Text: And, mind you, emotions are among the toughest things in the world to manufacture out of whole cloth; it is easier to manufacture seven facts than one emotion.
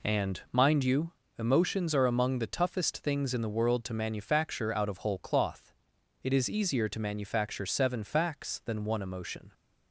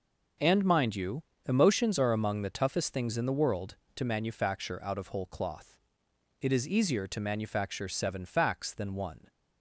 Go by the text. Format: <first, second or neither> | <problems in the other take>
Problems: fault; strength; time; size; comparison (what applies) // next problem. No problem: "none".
first | starts louder than the rest; until 1.6 s; 6.5 dB // stops before "emotion"; at 9.2 s